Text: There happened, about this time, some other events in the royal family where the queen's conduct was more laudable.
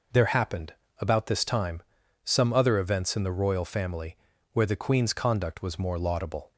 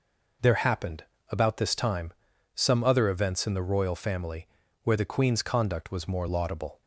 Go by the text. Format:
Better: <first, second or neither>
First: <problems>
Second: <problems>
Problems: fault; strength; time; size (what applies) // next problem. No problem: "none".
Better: neither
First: pauses between "family" and "where"; slight; at 4.1 s; 0.36 s long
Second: pauses between "family" and "where"; slight; at 4.4 s; 0.36 s long